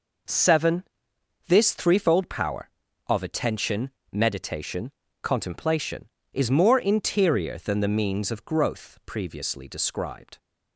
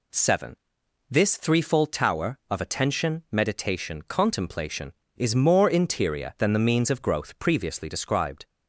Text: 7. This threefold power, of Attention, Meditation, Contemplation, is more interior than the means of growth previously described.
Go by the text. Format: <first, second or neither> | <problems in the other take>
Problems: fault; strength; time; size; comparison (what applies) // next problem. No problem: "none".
first | says "tower" for "power"; at 1.9 s